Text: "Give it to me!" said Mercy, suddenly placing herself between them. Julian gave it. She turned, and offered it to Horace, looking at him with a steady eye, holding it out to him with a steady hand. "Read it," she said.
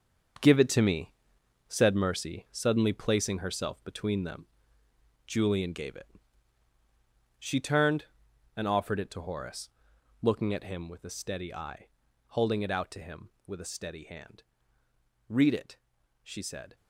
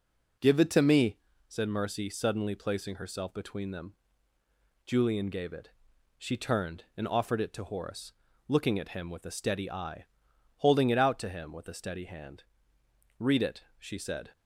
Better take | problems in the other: second | gets quieter; strong; throughout; 10 dB

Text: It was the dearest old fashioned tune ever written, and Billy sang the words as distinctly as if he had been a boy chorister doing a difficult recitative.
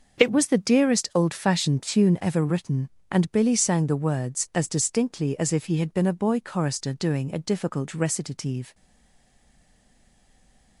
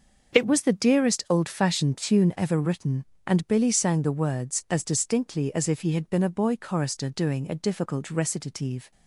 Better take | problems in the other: second | starts louder than the rest; until 1.2 s; 6.5 dB; also in the second // stays silent after the last word; noticeable; from 8.7 s on; 2.0 s long

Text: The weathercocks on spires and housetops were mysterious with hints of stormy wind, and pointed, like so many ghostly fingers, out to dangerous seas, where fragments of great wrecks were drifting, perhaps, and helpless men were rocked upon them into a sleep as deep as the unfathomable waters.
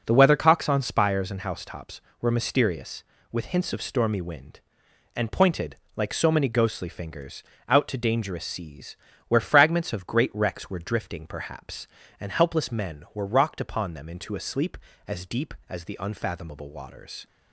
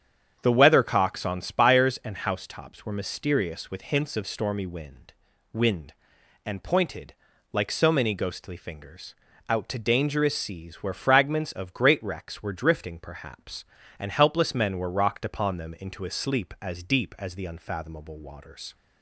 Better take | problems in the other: first | starts louder than the rest; strong; until 1.4 s; 8.5 dB // says "wind" twice; at 5.5 s

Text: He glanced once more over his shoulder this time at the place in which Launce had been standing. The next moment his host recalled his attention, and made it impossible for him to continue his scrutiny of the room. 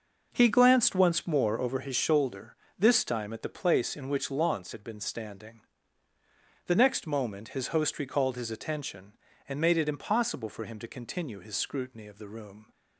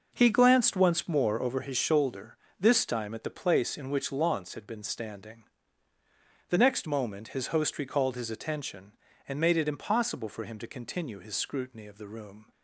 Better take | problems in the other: neither | pauses between "shoulder" and "this"; slight; the same in both

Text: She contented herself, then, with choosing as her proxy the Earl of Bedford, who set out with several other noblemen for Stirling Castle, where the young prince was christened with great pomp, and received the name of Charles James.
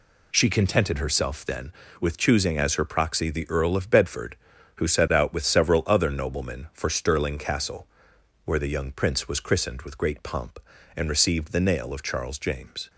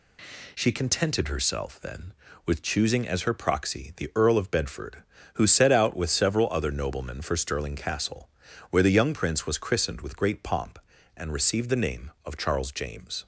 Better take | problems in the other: second | says "nail" for "name"; at 11.5 s

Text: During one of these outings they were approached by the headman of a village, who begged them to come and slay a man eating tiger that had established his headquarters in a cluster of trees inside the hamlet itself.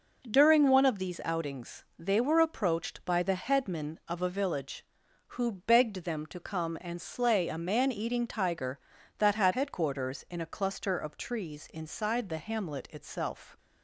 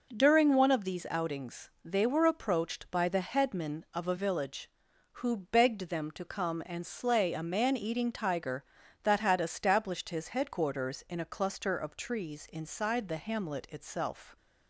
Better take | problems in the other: second | skips "established his"; at 9.5 s

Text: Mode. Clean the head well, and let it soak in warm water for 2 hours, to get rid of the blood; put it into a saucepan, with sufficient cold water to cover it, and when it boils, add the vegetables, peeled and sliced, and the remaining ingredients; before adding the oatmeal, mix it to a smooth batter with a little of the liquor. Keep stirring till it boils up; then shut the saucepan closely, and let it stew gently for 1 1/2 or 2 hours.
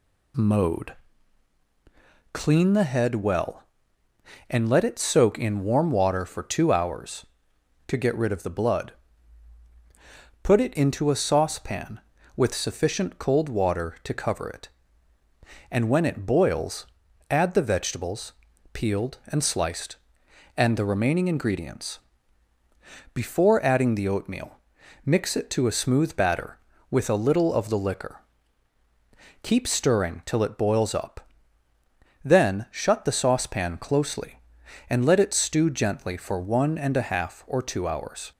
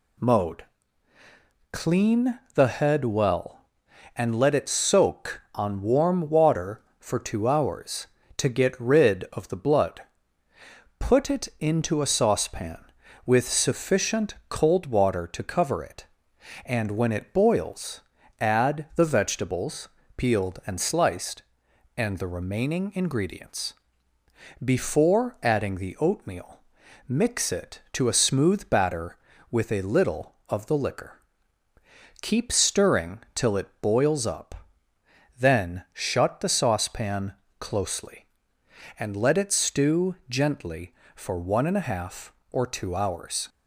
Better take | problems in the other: first | pauses between "Clean" and "the"; slight; at 2.3 s; 0.18 s long // says "on" for "in"; at 5.5 s // pauses between "saucepan" and "closely"; slight; at 37.3 s; 0.26 s long

